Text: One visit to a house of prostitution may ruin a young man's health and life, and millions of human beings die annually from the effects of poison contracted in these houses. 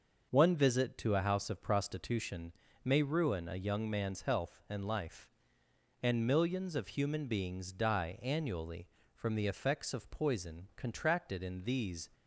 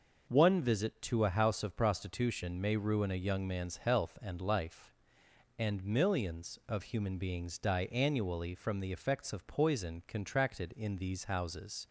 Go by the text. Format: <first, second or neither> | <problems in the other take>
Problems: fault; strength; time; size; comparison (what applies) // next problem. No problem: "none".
second | pauses between "prostitution" and "may"; slight; at 2.5 s; 0.32 s long // stops before "houses"; at 12.1 s